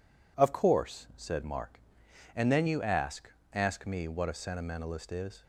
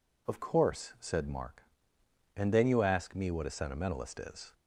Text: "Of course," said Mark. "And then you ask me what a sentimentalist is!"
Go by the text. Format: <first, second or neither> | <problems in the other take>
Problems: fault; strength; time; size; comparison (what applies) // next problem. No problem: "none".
second | says "ask" twice; at 3.5 s